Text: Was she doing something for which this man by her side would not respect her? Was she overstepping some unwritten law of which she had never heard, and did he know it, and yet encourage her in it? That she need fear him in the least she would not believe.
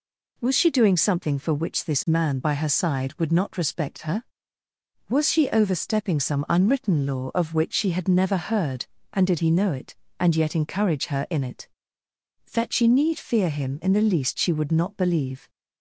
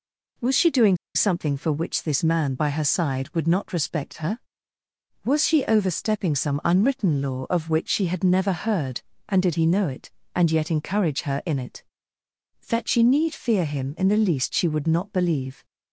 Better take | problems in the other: first | pauses between "doing" and "something"; slight; at 0.9 s; 0.18 s long

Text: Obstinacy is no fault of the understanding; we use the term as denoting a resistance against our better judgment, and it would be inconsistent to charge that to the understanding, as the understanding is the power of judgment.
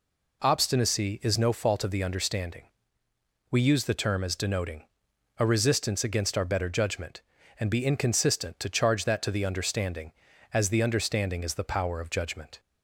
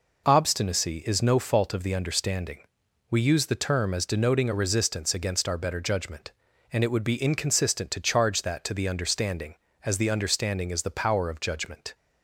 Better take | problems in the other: second | pauses between "denoting" and "a"; noticeable; at 4.8 s; 0.54 s long // skips "it would"; at 7.6 s

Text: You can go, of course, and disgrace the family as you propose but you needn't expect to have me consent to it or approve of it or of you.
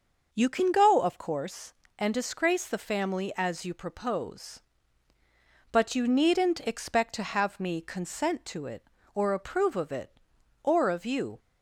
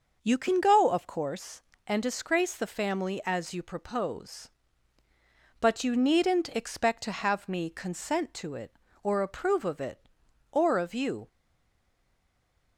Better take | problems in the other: first | starts louder than the rest; until 1.2 s; 6 dB; also in the first // stays silent after the last word; noticeable; from 11.2 s on; 1.5 s long

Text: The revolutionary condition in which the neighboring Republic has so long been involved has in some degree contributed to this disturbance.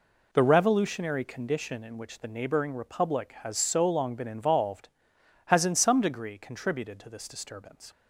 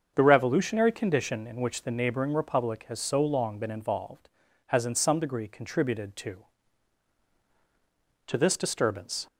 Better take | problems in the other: first | starts louder than the rest; until 1.1 s; 7 dB // says "to" twice; at 8.2 s

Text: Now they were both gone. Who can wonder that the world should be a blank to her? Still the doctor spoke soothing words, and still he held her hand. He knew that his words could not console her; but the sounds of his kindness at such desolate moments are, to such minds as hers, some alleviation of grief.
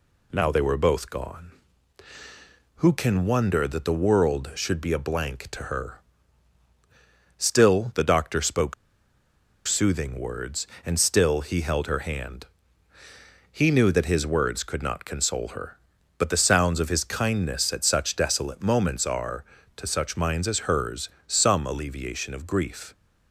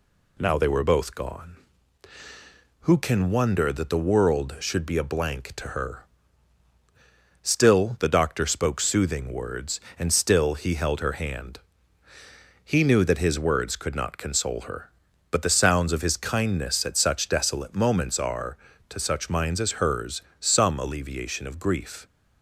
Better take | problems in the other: second | pauses between "spoke" and "soothing"; noticeable; at 8.7 s; 0.93 s long

